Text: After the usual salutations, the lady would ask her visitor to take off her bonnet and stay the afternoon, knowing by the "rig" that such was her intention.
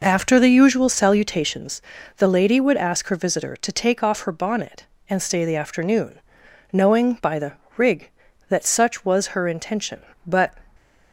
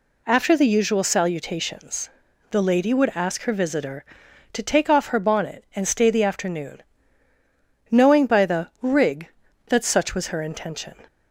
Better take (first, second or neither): second